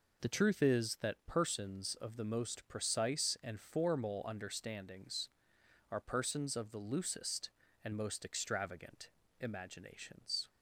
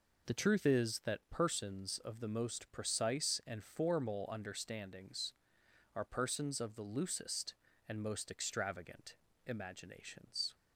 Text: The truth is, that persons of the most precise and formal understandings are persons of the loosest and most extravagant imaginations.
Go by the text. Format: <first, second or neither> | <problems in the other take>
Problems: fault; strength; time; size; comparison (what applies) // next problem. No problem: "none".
neither | pauses between "extravagant" and "imaginations"; slight; the same in both